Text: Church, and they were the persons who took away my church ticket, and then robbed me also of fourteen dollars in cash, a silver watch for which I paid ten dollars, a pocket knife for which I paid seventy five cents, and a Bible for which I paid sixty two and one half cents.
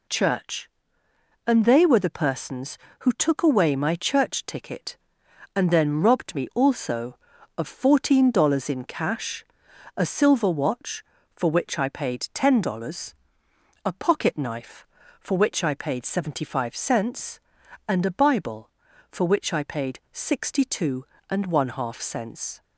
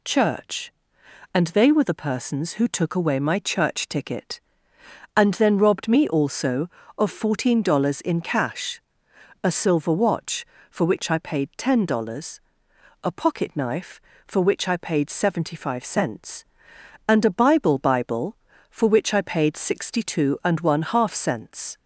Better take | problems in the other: first | says "Bible" twice; at 17.7 s

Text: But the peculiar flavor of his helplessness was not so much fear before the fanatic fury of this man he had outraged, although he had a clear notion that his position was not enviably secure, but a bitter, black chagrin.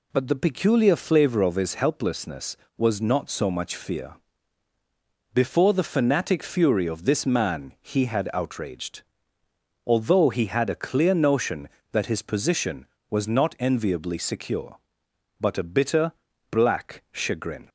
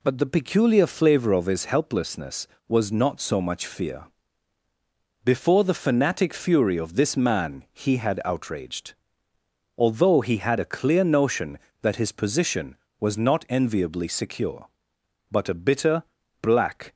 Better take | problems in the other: first | pauses between "fear" and "before"; at 4.0 s; 1.1 s long; also in the first // stops before "chagrin"; at 16.9 s

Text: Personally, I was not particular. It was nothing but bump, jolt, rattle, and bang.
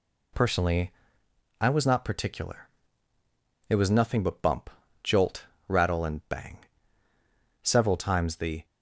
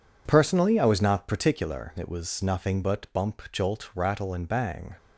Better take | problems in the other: second | goes on to say "Several times the"; noticeable; from 7.6 s on; 1.0 s long

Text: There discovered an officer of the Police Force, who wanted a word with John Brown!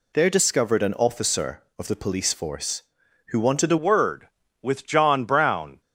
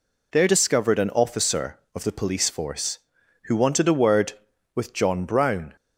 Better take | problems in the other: second | changes voice at "word"; from 3.7 s on; 2.1 s long

